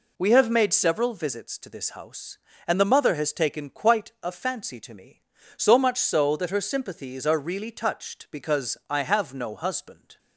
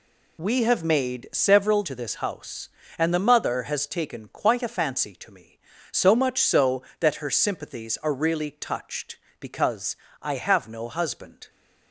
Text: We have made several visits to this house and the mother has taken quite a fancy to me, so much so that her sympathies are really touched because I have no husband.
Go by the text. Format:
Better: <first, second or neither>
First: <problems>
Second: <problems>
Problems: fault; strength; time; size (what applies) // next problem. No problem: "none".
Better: first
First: none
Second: skips "visits"; at 1.8 s // pauses between "because" and "I"; slight; at 9.9 s; 0.26 s long